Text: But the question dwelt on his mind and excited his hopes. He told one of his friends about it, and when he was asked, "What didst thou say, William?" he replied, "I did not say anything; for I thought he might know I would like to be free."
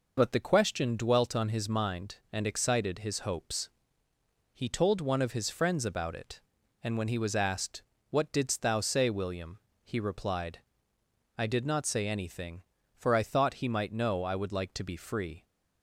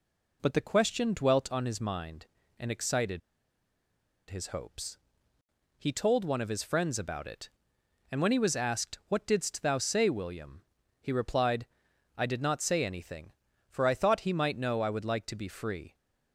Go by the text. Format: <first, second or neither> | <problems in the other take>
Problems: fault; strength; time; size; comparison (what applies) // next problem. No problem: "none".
first | pauses between "excited" and "his"; at 3.2 s; 1.1 s long